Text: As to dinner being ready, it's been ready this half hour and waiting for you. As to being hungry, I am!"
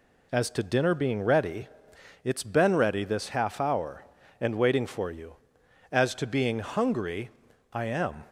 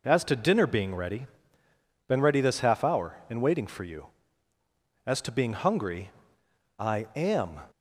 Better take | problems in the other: first | skips "it's"; at 1.6 s

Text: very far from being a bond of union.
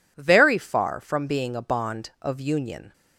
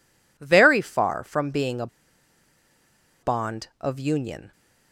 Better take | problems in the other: first | pauses between "a" and "bond"; strong; at 1.8 s; 1.3 s long

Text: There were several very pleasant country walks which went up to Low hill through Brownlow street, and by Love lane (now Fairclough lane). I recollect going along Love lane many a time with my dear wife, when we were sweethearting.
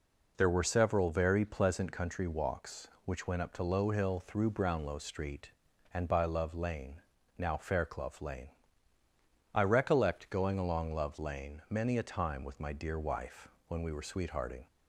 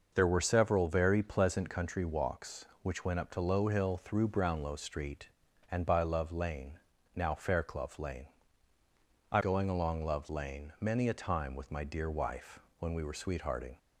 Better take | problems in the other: first | skips "recollect"; at 9.4 s

